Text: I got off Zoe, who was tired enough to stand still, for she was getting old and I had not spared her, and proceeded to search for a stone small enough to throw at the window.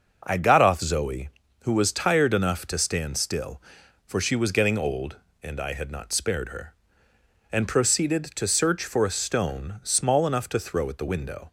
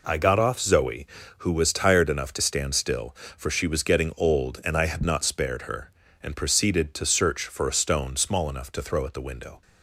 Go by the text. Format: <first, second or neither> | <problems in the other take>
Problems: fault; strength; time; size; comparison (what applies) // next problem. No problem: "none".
neither | none